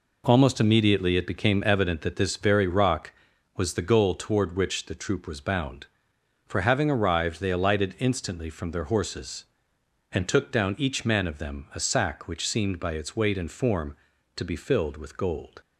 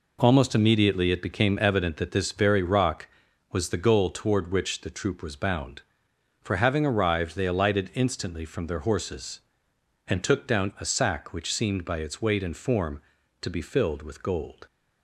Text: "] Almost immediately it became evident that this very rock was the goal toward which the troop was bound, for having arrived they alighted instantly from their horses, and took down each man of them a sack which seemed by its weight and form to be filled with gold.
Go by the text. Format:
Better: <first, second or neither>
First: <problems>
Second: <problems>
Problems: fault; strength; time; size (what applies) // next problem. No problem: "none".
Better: first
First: none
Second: skips "each man of them"; at 10.7 s